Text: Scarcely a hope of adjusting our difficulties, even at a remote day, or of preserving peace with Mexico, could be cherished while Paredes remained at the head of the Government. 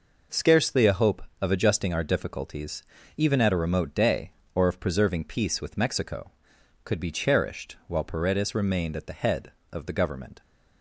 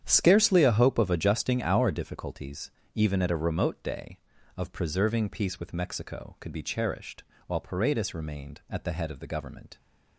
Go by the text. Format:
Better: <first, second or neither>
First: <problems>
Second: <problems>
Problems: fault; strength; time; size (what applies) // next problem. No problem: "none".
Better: first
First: none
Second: starts louder than the rest; strong; until 1.0 s; 9 dB // skips "or"; at 4.3 s // pauses between "cherished" and "while"; slight; at 7.2 s; 0.24 s long